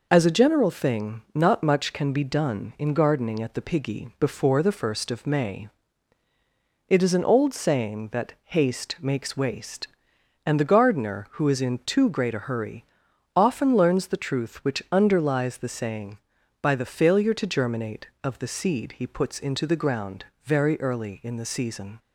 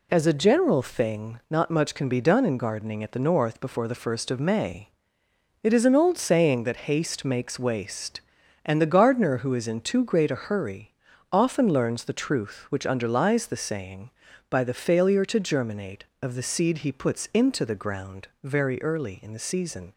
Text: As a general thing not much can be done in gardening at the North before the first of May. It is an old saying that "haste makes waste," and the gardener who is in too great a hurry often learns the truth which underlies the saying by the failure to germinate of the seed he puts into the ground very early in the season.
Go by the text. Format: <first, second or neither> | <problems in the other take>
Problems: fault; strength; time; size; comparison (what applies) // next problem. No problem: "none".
second | says "Piggy" for "North"; at 3.6 s // pauses between "hurry" and "often"; noticeable; at 12.8 s; 0.50 s long; slight in the second // pauses between "ground" and "very"; slight; at 20.2 s; 0.18 s long; slight in the second